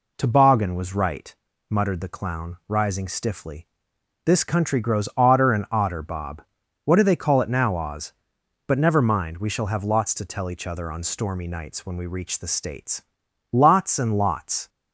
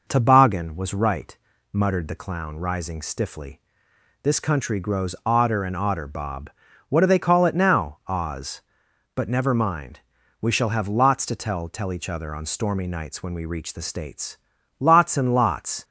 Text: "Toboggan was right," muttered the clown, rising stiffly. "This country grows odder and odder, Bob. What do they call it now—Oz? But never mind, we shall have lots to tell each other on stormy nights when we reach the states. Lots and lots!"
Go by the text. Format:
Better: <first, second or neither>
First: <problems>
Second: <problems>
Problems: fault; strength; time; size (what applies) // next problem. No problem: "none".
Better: first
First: none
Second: says "tell" twice; at 11.6 s